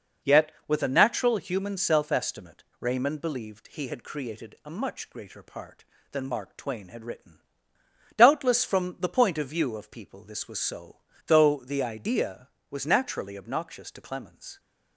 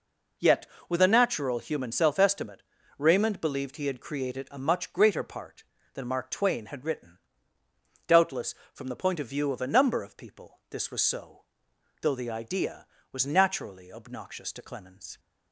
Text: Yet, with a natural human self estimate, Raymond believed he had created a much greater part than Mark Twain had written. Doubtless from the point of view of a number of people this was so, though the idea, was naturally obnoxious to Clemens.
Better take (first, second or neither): second